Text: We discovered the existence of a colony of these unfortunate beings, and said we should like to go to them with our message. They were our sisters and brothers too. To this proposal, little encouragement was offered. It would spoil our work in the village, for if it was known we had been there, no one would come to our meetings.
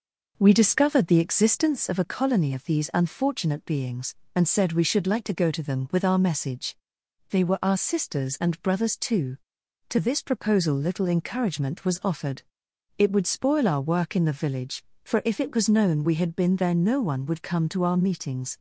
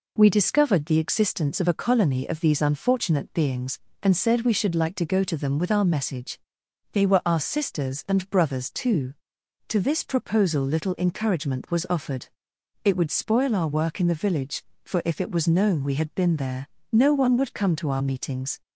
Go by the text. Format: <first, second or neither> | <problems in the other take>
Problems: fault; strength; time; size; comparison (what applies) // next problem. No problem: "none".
second | starts louder than the rest; noticeable; until 1.9 s; 5.5 dB